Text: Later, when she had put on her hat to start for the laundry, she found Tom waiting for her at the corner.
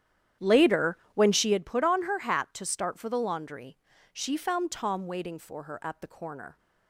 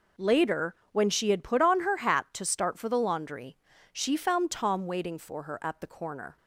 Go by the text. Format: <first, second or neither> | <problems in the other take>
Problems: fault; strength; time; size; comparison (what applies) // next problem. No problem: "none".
second | starts louder than the rest; strong; until 1.6 s; 10 dB